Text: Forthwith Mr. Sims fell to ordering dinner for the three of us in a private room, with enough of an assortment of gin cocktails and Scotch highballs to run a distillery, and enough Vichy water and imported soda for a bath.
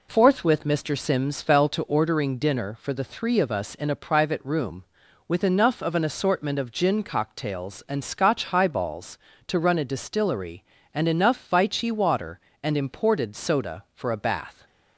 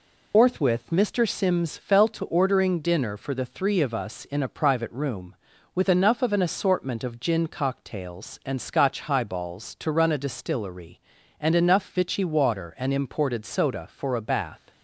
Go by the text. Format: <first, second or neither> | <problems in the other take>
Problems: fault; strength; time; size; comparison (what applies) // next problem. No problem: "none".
first | loses the start of "Forthwith"; at 0.3 s; 160 ms